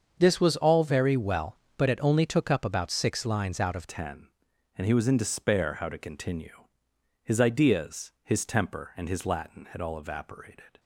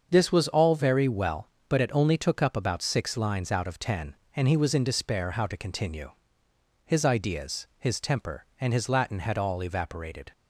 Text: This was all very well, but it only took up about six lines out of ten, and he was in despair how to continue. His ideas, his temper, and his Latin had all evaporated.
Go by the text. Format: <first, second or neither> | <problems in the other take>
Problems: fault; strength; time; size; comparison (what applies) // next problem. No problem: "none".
second | starts louder than the rest; until 1.2 s; 6.5 dB; also in the second // changes voice at "ten"; from 3.8 s on; 6.9 s long